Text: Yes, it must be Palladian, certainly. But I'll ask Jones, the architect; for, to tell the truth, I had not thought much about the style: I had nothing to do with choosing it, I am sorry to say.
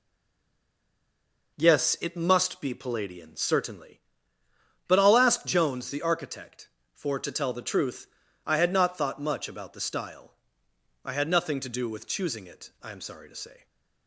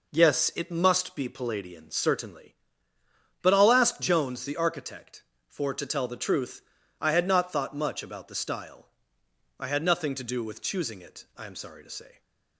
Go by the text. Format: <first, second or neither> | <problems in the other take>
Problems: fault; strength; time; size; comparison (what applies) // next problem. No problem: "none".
second | stays silent before the first word; noticeable; until 1.5 s; 1.5 s long